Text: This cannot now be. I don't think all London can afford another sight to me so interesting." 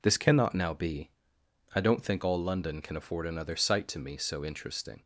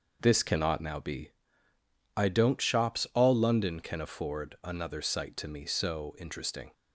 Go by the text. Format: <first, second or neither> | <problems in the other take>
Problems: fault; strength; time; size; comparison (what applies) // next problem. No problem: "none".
first | says "shops" for "think"; at 2.6 s